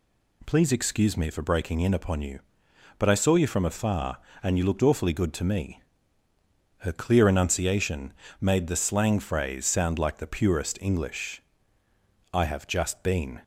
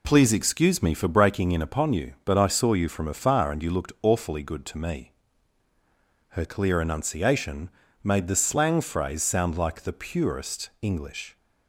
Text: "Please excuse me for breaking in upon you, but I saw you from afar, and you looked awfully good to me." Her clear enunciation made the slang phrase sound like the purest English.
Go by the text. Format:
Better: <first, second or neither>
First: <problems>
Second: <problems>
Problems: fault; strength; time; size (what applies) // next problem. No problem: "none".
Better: second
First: pauses between "enunciation" and "made"; slight; at 8.1 s; 0.28 s long // goes on to say "I have just been"; noticeable; from 12.3 s on; 1.0 s long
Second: pauses between "enunciation" and "made"; slight; at 7.7 s; 0.32 s long